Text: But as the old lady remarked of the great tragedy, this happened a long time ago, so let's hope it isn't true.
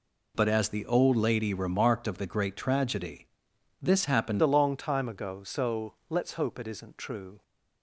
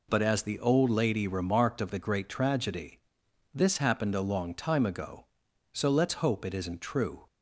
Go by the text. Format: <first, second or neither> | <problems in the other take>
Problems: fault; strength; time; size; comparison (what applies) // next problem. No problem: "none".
second | changes voice at "a"; from 4.4 s on; 3.0 s long // pauses between "so" and "let's"; slight; at 5.9 s; 0.16 s long